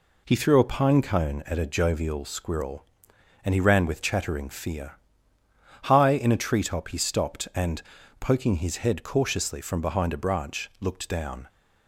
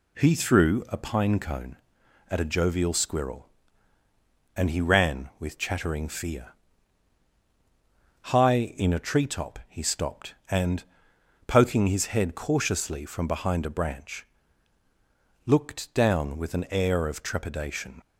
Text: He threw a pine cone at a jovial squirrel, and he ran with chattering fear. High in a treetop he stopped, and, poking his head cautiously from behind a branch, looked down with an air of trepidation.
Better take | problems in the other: second | stops before "with an air of trepidation"; at 11.4 s

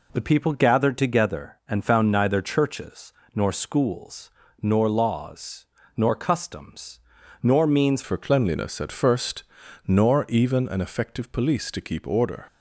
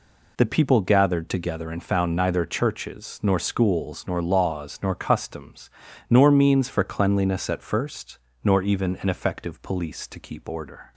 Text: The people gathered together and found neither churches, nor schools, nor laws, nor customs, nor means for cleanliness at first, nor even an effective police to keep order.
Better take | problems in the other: second | changes voice at "for"; from 8.0 s on; 4.4 s long

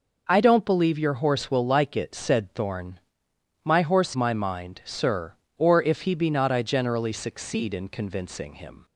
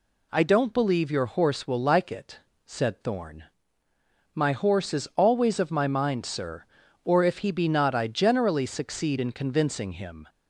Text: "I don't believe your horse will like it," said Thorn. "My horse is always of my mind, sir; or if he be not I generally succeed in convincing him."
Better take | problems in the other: second | skips "is always of"; at 4.1 s

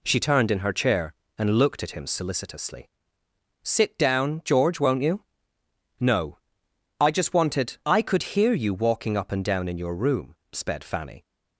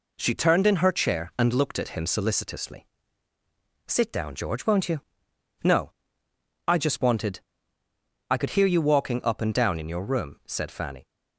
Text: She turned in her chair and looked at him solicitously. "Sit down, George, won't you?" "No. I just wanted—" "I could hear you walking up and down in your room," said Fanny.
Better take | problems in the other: second | says "sped" for "said"; at 10.5 s

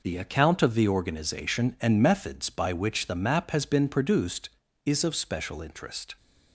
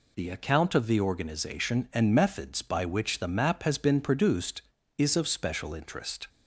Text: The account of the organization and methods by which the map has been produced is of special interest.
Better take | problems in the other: second | gets quieter; noticeable; throughout; 6 dB

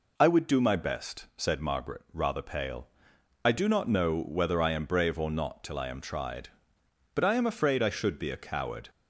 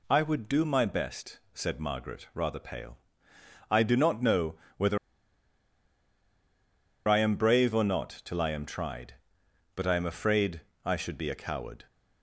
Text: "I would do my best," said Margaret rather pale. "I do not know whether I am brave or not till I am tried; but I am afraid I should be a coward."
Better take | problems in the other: first | pauses between "know" and "whether"; slight; at 4.5 s; 0.24 s long // pauses between "whether" and "I"; strong; at 4.9 s; 2.1 s long // pauses between "afraid" and "I"; slight; at 10.6 s; 0.24 s long

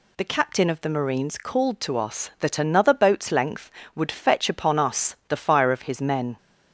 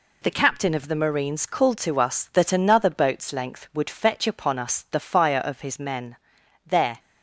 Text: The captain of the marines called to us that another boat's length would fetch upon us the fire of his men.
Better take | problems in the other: first | goes on to say "There"; slight; from 6.6 s on; 0.34 s long

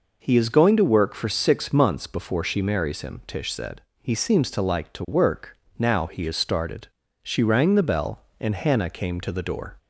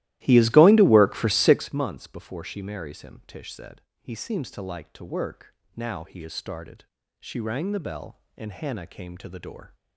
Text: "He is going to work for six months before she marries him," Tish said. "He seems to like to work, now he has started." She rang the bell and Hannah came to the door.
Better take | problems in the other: first | starts louder than the rest; strong; until 1.7 s; 16 dB

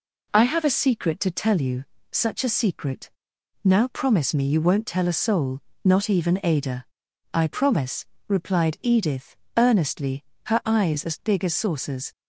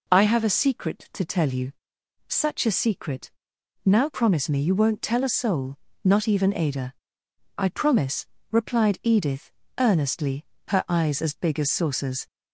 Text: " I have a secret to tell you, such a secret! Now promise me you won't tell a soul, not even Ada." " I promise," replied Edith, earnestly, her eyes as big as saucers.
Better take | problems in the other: neither | none

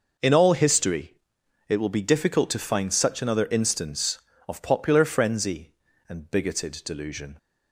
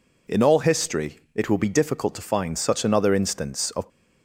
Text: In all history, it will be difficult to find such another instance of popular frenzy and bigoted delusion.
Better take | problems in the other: first | stops before "popular frenzy and bigoted delusion"; at 3.9 s

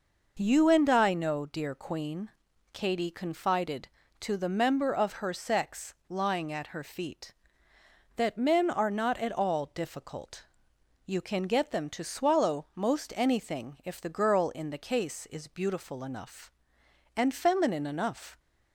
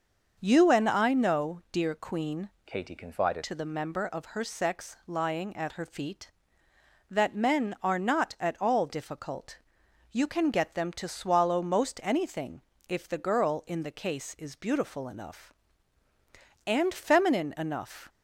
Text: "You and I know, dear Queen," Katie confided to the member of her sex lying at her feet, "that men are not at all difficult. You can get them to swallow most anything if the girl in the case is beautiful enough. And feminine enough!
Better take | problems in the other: first | starts louder than the rest; until 1.4 s; 6.5 dB // changes voice from "Katie" to "confided"; from 2.6 to 3.4 s; 0.8 s long // pauses between "anything" and "if"; slight; at 12.6 s; 0.26 s long

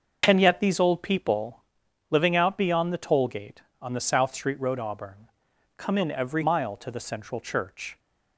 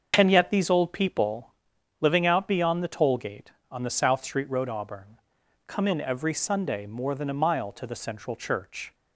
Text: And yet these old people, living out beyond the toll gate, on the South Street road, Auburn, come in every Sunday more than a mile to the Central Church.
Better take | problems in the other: second | starts louder than the rest; until 1.2 s; 6 dB; also in the second // skips "Sunday more than a"; at 6.4 s

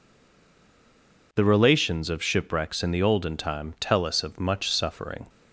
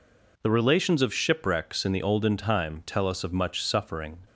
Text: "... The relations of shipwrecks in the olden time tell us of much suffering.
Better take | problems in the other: second | stays silent before the first word; noticeable; until 1.3 s; 1.3 s long

